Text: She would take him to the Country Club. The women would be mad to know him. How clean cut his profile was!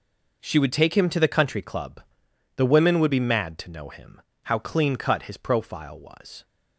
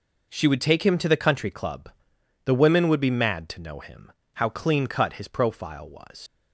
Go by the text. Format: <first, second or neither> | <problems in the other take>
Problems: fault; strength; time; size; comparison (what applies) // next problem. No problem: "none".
first | leaves "was" unfinished; at 6.2 s; 80 ms